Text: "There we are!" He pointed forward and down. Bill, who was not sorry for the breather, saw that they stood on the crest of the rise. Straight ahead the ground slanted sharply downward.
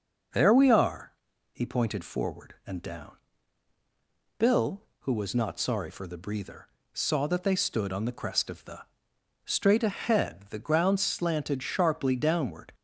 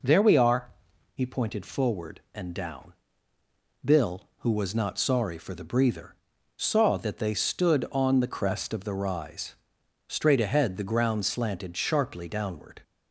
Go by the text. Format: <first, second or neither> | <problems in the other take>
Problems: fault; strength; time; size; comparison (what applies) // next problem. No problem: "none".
second | skips "rise"; at 9.1 s